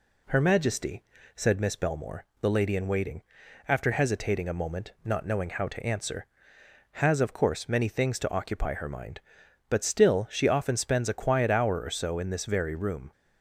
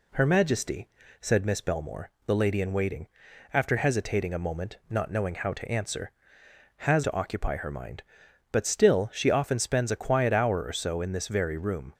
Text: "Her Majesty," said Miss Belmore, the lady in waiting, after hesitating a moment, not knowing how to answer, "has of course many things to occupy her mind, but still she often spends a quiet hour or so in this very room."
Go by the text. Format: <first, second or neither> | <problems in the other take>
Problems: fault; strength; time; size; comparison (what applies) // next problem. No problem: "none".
first | skips "of course many things"; at 7.0 s